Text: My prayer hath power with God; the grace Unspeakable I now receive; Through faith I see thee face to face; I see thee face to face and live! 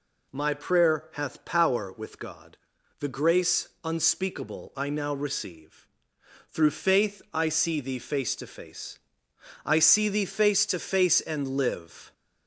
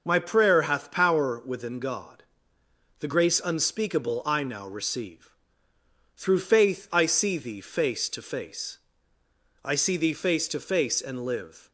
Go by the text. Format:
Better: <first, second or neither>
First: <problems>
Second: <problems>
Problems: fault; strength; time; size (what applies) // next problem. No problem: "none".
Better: first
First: none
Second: starts louder than the rest; until 1.0 s; 6 dB // says "within" for "with"; at 1.4 s